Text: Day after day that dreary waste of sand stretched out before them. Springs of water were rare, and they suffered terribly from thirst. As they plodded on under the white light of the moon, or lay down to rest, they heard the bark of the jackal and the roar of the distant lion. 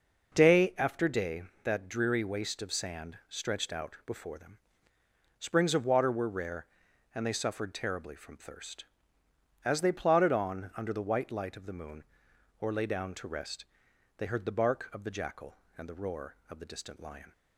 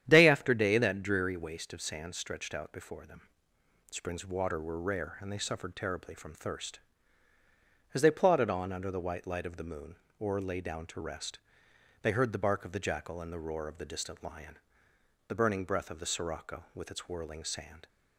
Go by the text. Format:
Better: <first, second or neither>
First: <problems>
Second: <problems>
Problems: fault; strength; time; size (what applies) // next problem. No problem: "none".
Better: first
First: none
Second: starts louder than the rest; strong; until 1.0 s; 10 dB // goes on to say "The burning breath of the sirocco with its whirling sand"; strong; from 15.2 s on; 2.6 s long